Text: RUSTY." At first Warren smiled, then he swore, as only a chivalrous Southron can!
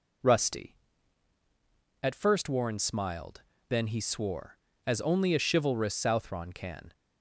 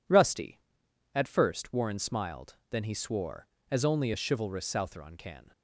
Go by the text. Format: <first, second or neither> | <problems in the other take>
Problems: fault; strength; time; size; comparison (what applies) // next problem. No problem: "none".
neither | none